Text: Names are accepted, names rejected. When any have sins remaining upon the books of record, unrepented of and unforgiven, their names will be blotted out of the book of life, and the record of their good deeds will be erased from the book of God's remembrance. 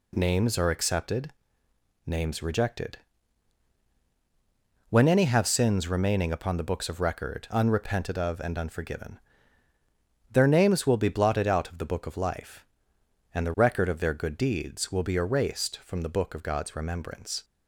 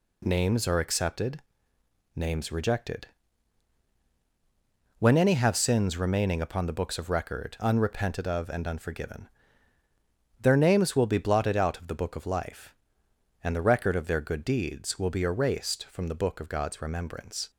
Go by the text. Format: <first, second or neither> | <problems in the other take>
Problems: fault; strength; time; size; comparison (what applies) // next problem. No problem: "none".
neither | none